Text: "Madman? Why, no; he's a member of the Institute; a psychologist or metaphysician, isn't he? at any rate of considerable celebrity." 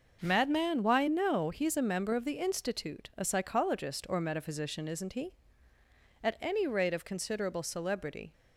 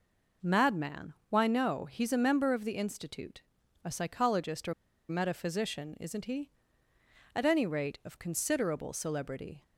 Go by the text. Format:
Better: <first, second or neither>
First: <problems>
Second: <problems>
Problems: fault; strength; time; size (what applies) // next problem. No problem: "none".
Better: first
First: none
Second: pauses between "or" and "metaphysician"; at 4.7 s; 0.37 s long